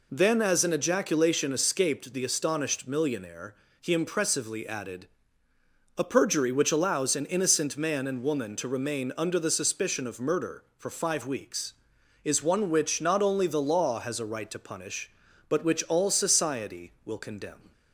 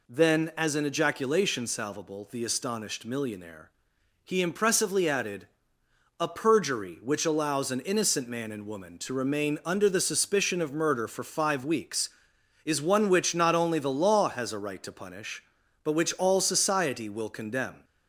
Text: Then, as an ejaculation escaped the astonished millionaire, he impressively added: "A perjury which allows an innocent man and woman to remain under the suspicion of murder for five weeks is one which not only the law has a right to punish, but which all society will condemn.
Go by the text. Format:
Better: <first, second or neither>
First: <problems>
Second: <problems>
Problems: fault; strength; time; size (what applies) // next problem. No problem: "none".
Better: first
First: none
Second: says "salvable" for "escaped"; at 1.6 s